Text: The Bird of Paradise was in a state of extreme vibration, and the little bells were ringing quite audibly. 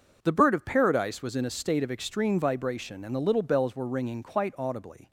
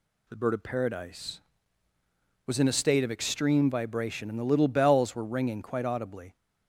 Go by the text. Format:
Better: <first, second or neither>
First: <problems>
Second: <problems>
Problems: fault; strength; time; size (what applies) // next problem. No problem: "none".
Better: neither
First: none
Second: none